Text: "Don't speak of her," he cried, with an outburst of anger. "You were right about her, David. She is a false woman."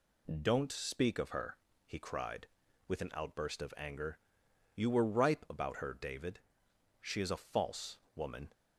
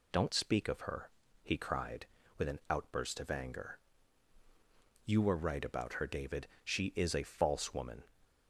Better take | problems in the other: second | says "ripe" for "right"; at 5.0 s // pauses between "false" and "woman"; slight; at 7.9 s; 0.16 s long

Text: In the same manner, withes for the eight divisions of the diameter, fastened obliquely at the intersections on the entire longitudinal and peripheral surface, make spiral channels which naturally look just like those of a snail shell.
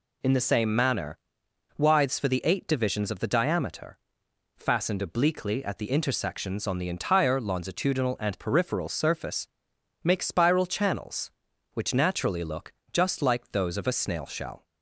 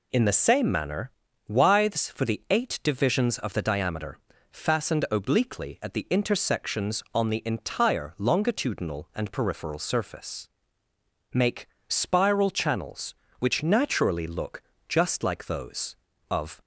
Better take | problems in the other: first | pauses between "make" and "spiral"; slight; at 11.6 s; 0.20 s long // pauses between "look" and "just"; slight; at 14.6 s; 0.30 s long; slight in the first // stops before "a snail shell"; at 16.6 s

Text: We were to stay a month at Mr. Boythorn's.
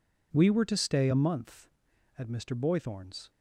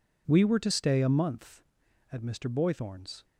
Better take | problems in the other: neither | none

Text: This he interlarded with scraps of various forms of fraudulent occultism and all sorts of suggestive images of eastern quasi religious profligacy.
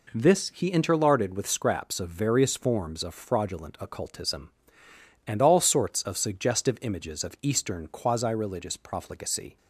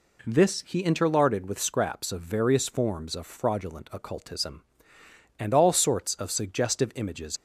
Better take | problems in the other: first | stops before "of eastern quasi religious profligacy"; at 7.3 s

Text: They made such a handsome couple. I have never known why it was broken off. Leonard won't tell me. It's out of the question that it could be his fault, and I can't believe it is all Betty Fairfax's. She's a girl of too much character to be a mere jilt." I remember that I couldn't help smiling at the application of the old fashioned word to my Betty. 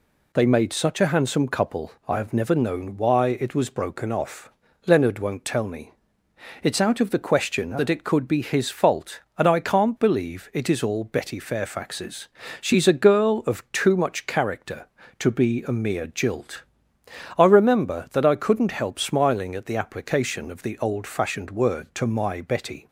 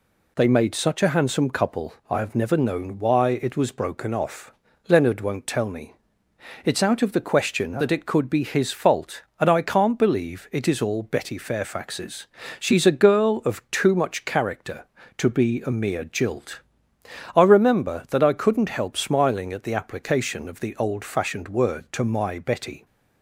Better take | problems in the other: neither | none

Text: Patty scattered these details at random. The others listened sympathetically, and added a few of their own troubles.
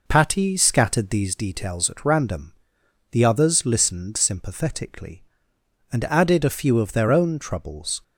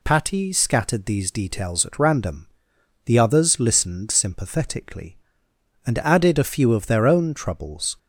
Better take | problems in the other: second | starts louder than the rest; noticeable; until 1.4 s; 5 dB

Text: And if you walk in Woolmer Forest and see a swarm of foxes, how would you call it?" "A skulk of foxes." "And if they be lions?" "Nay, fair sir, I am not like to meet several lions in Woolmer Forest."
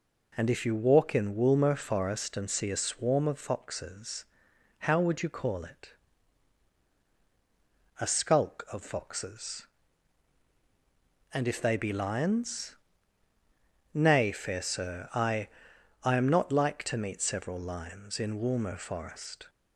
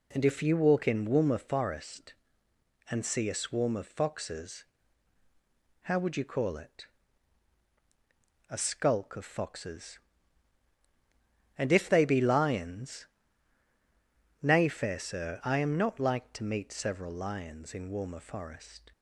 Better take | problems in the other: second | says "I" twice; at 16.0 s

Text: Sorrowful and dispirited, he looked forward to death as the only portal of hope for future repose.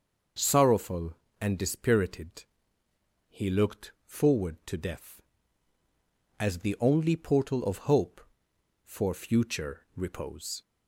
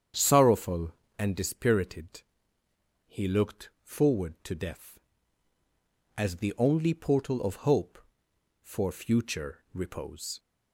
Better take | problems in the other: first | starts louder than the rest; strong; until 1.3 s; 8 dB

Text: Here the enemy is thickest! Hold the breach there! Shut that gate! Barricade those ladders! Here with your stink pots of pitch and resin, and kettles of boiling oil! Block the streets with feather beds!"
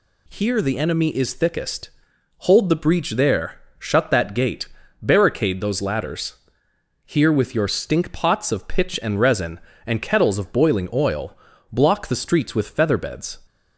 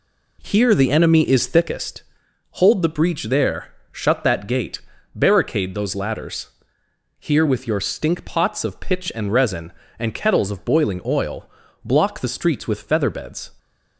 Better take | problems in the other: first | starts louder than the rest; slight; until 1.8 s; 2.5 dB

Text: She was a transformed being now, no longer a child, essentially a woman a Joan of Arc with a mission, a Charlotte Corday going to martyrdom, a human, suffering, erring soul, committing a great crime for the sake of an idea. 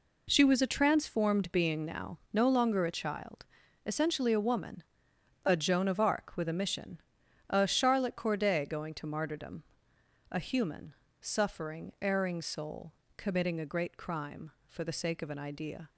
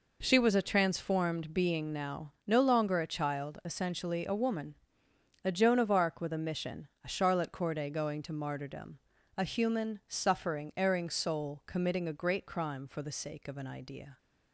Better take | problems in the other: neither | pauses between "woman" and "a"; noticeable; the same in both

